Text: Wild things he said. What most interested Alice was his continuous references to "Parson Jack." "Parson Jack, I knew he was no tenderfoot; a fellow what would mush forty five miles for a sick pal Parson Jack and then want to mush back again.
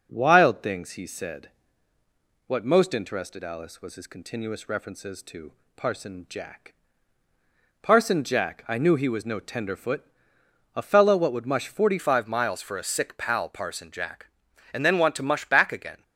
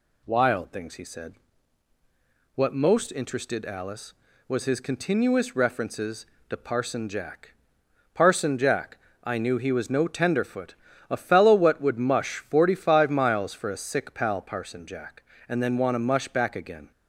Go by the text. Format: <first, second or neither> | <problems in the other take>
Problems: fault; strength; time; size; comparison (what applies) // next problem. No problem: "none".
second | pauses between "to" and "Parson"; slight; at 5.5 s; 0.24 s long // changes voice at "five"; from 11.9 s on; 4.1 s long